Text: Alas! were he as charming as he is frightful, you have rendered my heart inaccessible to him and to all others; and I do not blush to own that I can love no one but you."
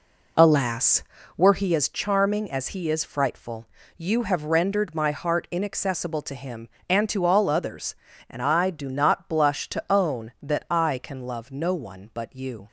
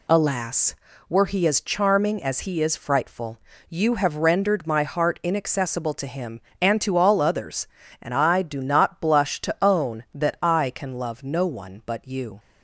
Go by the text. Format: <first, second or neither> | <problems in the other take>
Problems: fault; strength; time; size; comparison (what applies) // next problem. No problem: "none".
second | starts louder than the rest; until 1.7 s; 3.5 dB